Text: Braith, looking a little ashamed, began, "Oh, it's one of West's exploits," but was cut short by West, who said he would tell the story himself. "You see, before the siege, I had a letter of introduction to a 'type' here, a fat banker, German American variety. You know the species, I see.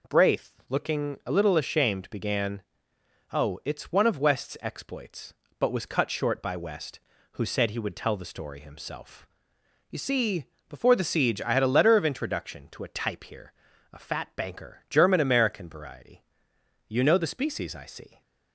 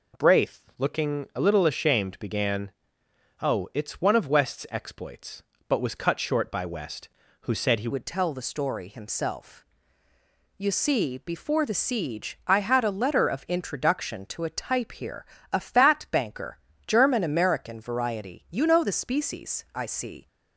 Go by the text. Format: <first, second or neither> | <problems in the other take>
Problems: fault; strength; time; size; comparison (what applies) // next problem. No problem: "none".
first | changes voice at "would"; from 7.9 s on; 12.3 s long